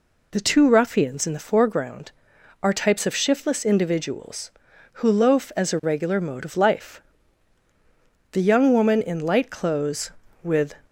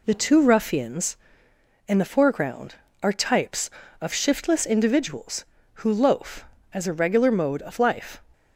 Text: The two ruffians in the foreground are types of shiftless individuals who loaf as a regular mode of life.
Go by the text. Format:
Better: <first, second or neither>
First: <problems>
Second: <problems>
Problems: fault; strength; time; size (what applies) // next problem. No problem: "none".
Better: second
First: goes on to say "The young woman in light clothes with"; strong; from 8.3 s on; 2.4 s long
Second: none